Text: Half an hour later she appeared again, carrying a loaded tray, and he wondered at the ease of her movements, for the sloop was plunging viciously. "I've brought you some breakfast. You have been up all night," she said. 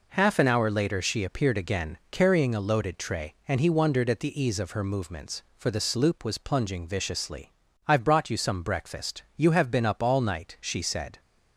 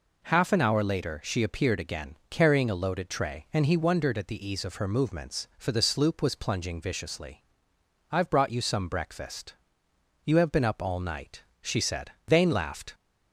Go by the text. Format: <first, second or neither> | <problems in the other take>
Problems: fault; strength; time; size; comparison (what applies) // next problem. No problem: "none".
first | goes on to say "Vane laughed"; noticeable; from 12.2 s on; 0.66 s long